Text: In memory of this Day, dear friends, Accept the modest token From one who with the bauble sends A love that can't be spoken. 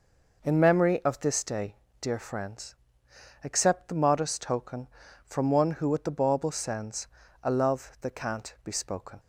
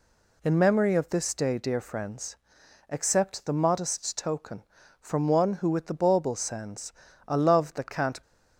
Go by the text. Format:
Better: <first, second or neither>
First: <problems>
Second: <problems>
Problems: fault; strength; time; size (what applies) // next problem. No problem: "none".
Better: first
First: pauses between "sends" and "A"; slight; at 7.0 s; 0.36 s long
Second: pauses between "sends" and "A"; slight; at 6.9 s; 0.34 s long // stops before "be spoken"; at 8.2 s